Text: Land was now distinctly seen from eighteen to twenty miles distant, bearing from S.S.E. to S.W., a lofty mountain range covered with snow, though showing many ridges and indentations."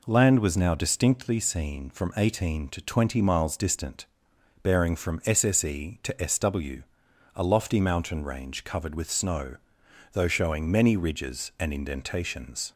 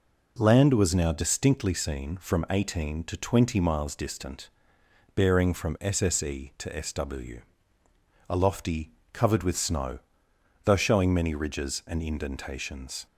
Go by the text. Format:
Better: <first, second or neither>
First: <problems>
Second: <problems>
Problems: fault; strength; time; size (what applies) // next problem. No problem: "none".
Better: first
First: none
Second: skips "mountain range"; at 9.0 s